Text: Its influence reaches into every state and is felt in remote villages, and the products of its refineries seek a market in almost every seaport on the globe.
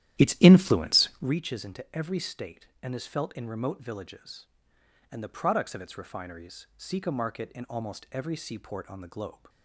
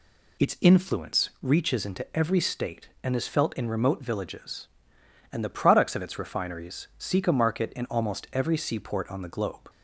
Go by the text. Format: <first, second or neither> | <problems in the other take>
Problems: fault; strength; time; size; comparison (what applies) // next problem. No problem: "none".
second | starts louder than the rest; strong; until 1.3 s; 12 dB